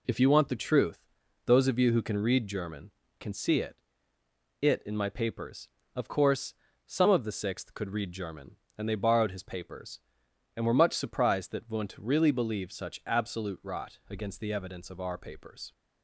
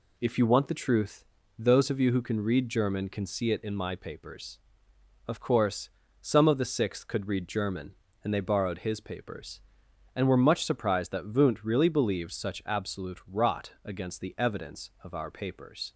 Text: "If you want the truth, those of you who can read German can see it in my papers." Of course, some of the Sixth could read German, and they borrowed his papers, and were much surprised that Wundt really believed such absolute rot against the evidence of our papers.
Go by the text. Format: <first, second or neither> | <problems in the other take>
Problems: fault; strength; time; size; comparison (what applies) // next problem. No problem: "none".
second | says "it" twice; at 4.6 s